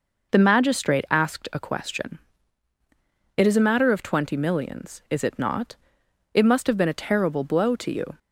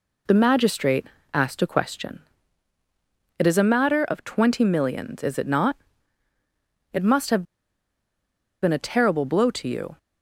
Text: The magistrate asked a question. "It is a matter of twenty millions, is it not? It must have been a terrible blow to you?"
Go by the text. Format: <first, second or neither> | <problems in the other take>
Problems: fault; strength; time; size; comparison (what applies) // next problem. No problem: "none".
first | pauses between "magistrate" and "asked"; slight; at 1.0 s; 0.26 s long // pauses between "have" and "been"; at 7.4 s; 1.1 s long